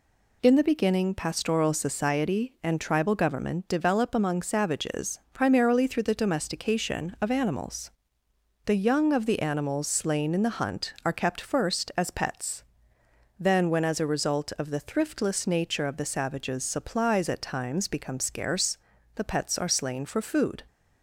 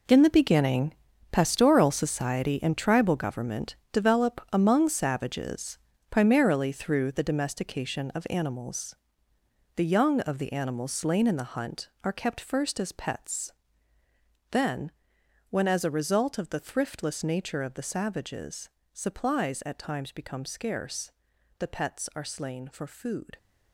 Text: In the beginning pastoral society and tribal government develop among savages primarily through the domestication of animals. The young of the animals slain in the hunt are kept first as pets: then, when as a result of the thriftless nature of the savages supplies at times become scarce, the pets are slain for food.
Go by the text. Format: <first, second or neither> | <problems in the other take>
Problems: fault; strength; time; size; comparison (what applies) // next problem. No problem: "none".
first | gets quieter; strong; throughout; 12 dB // pauses between "beginning" and "pastoral"; at 0.9 s; 0.38 s long // pauses between "government" and "develop"; slight; at 3.7 s; 0.16 s long // pauses between "savages" and "primarily"; slight; at 5.7 s; 0.32 s long // pauses between "savages" and "supplies"; slight; at 18.6 s; 0.24 s long